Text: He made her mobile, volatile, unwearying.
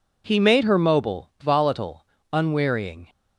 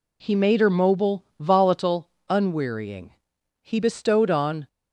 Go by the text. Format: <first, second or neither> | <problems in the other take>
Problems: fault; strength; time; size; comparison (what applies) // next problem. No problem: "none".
first | goes on to say "He bestowed on"; noticeable; from 3.6 s on; 1.0 s long